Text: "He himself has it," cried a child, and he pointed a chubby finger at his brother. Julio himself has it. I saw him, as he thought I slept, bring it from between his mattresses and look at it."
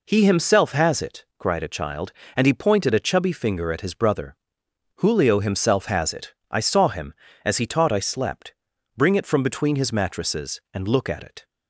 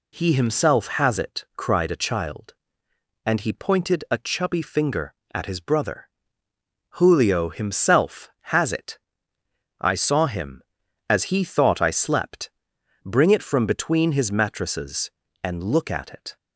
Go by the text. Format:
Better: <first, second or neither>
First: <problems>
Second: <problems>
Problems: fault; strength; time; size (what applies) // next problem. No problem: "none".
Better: second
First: says "taught" for "thought"; at 7.6 s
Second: none